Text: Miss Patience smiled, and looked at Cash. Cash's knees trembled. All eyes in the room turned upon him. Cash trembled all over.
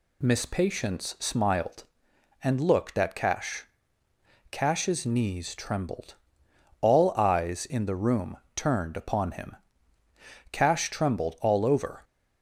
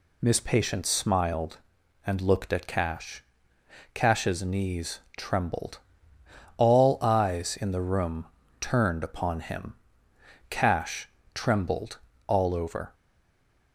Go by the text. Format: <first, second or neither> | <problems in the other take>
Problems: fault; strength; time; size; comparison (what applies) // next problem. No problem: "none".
first | pauses between "knees" and "trembled"; slight; at 4.9 s; 0.18 s long // pauses between "room" and "turned"; slight; at 8.2 s; 0.36 s long; slight in the first // pauses between "Cash" and "trembled"; slight; at 11.0 s; 0.24 s long // pauses between "trembled" and "all"; slight; at 11.9 s; 0.30 s long // stays silent after the last word; slight; from 12.9 s on; 0.8 s long